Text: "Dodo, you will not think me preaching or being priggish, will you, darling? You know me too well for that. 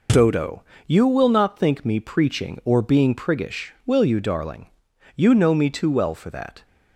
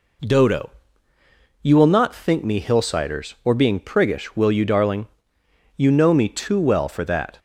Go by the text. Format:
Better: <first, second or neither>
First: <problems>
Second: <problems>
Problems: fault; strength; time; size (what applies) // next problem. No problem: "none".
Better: first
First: none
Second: says "hillsiders" for "preaching"; at 2.6 s